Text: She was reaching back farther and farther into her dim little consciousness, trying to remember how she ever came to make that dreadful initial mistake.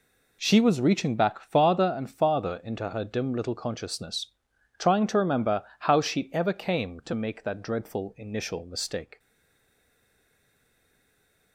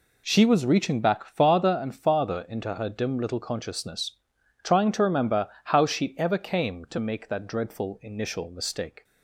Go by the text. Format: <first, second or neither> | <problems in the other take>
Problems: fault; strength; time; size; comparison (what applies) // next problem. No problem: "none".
second | pauses between "remember" and "how"; slight; at 5.6 s; 0.16 s long; slight in the second // stays silent after the last word; from 9.1 s on; 2.4 s long